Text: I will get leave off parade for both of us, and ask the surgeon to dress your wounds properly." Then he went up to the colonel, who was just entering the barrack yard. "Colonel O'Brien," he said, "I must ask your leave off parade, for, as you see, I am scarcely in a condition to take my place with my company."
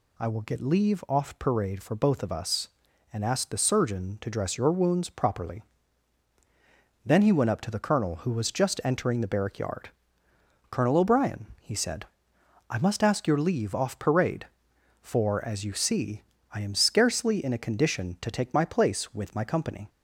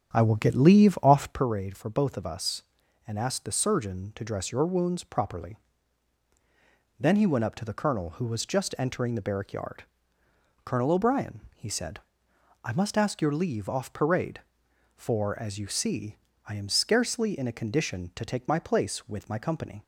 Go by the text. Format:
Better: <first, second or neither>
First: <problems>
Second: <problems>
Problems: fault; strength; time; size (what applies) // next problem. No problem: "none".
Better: first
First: none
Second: starts louder than the rest; strong; until 1.5 s; 8.5 dB